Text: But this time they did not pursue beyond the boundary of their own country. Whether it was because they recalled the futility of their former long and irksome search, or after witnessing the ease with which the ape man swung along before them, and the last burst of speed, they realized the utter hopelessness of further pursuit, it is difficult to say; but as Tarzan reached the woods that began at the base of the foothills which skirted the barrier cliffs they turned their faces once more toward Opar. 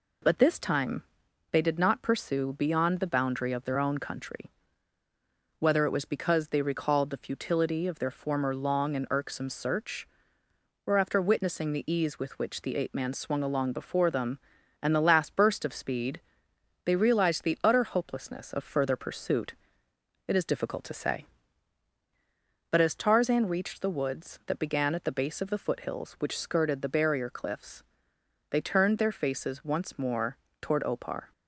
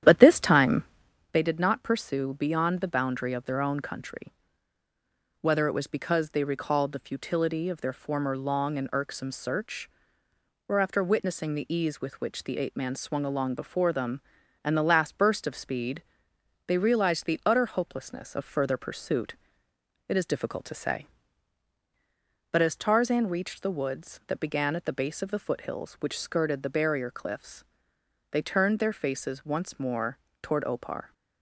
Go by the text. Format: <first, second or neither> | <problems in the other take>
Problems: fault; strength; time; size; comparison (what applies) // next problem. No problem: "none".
first | starts louder than the rest; strong; until 1.3 s; 10.5 dB // pauses between "time" and "they"; noticeable; at 0.8 s; 0.48 s long; noticeable in the first // pauses between "cliffs" and "they"; noticeable; at 27.6 s; 0.68 s long; noticeable in the first // pauses between "more" and "toward"; slight; at 30.1 s; 0.24 s long; slight in the first